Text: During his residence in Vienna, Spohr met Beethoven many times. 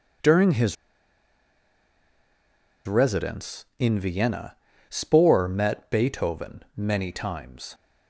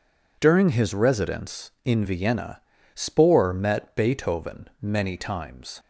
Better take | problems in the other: second | pauses between "his" and "residence"; strong; at 0.7 s; 2.1 s long

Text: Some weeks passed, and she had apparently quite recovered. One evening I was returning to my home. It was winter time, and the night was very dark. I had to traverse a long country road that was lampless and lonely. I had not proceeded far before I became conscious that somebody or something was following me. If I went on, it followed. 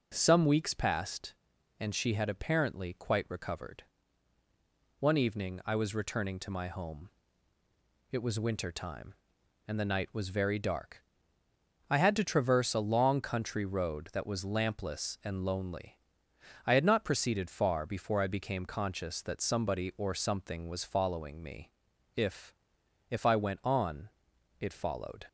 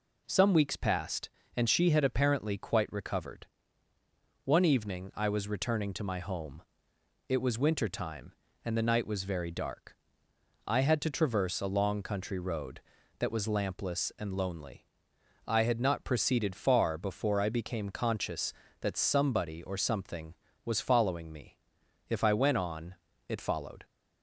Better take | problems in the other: second | says "If" twice; at 23.0 s

